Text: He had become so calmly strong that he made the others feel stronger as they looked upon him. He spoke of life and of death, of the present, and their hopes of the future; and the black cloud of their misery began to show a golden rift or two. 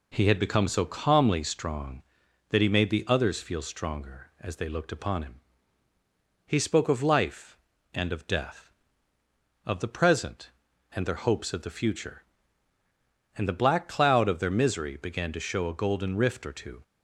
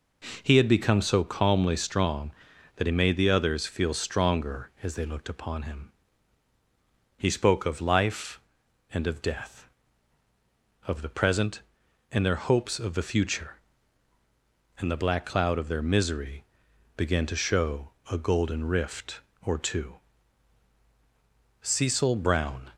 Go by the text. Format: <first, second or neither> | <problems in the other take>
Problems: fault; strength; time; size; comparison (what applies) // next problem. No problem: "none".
first | pauses between "misery" and "began"; noticeable; at 16.4 s; 0.50 s long // pauses between "show" and "a"; slight; at 17.9 s; 0.18 s long // goes on to say "Cecil Brown"; noticeable; from 21.6 s on; 1.1 s long